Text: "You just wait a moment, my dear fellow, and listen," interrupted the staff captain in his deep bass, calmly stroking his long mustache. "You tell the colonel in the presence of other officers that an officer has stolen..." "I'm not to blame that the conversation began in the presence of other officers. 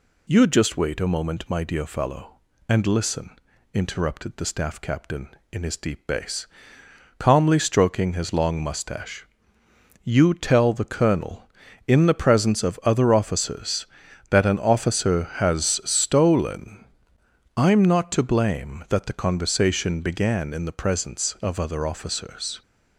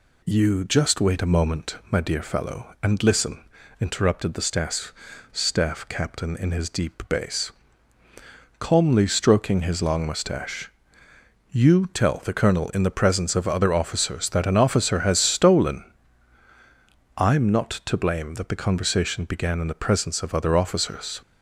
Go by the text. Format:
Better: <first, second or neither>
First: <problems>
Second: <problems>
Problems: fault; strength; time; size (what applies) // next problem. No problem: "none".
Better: first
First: none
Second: says "staff" twice; at 5.3 s